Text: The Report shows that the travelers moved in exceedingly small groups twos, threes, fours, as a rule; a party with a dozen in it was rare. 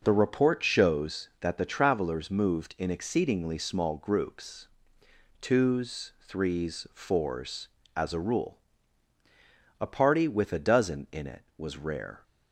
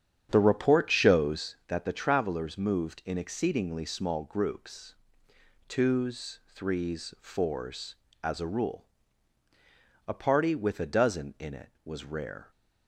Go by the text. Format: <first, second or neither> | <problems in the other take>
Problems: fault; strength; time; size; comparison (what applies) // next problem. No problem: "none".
first | starts louder than the rest; strong; until 1.6 s; 9 dB // pauses between "groups" and "twos"; noticeable; at 4.9 s; 0.72 s long; noticeable in the first